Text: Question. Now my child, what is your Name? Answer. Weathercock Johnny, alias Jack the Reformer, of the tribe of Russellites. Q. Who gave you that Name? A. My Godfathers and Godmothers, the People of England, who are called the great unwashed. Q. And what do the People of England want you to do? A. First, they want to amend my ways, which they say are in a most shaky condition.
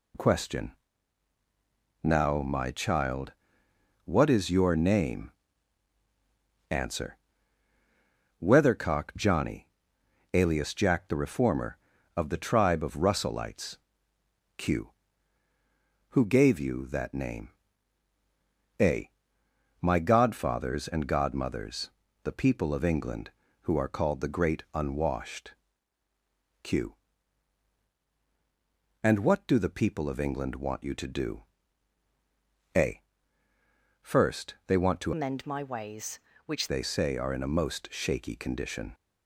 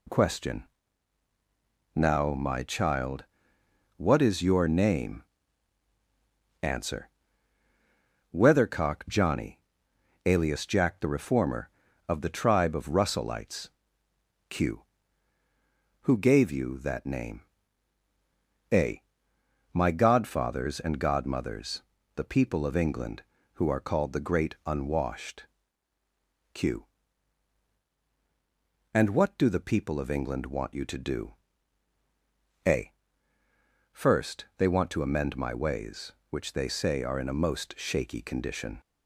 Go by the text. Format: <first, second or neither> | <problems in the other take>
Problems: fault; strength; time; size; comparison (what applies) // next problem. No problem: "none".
second | changes voice from "amend" to "which"; from 35.1 to 36.6 s; 1.5 s long